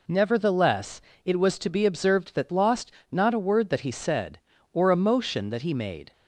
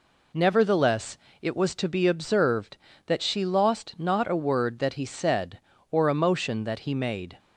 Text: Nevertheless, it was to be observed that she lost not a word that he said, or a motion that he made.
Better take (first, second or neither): second